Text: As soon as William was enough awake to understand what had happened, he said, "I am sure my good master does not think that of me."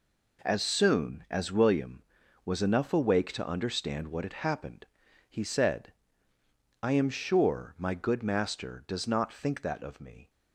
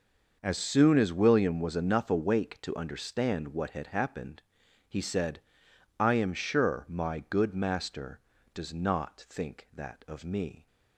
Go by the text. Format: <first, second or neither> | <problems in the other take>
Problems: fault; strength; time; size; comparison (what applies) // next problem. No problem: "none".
neither | none